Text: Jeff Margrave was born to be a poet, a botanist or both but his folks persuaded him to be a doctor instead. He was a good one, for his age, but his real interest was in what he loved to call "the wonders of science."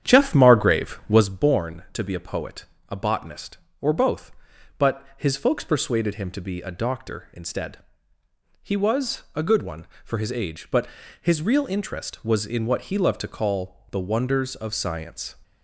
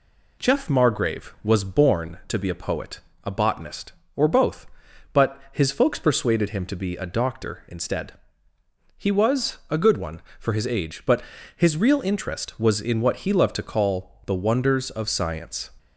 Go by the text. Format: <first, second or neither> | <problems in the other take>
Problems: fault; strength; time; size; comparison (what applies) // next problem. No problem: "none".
second | starts louder than the rest; strong; until 1.3 s; 9 dB // pauses between "but" and "his"; slight; at 10.8 s; 0.34 s long; slight in the second